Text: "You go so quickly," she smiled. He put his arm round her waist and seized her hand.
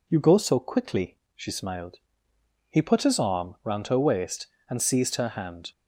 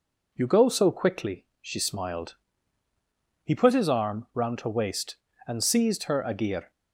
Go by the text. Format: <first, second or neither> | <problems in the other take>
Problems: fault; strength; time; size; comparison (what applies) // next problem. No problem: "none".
first | says "agir" for "hand"; at 6.2 s